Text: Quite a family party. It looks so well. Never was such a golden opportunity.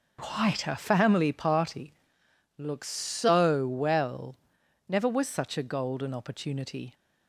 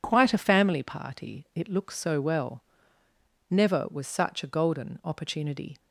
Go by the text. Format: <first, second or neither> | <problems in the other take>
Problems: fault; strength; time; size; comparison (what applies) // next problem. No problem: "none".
second | skips "It"; at 2.2 s